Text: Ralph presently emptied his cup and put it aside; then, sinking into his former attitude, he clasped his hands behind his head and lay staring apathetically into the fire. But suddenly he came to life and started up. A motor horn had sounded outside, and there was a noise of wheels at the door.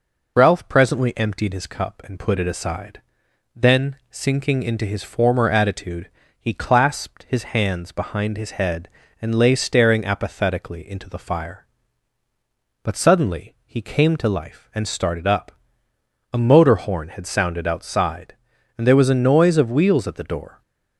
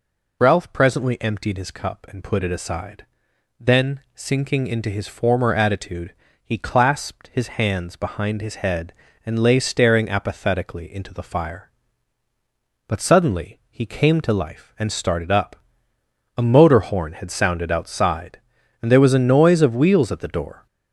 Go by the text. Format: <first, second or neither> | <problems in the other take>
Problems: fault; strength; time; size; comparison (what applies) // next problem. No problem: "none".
first | gets louder; noticeable; throughout; 5 dB